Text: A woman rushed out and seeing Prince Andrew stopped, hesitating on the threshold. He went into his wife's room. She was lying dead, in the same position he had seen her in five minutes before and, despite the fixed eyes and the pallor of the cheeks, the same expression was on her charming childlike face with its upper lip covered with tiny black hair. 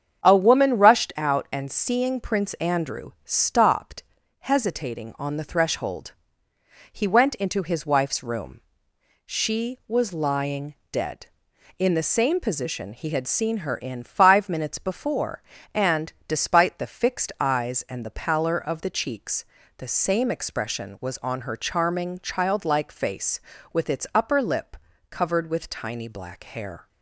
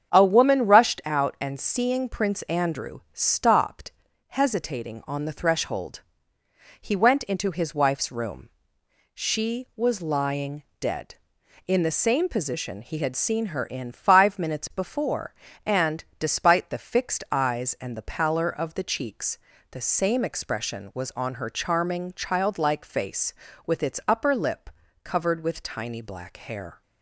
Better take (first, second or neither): neither